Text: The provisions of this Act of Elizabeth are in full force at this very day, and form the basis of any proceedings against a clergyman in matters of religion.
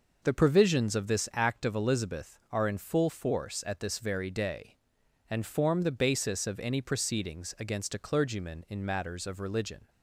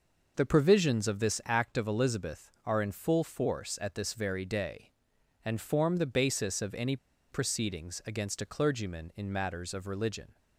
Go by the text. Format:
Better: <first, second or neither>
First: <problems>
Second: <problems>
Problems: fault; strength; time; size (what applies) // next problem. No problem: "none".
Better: first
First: none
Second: pauses between "any" and "proceedings"; slight; at 6.9 s; 0.35 s long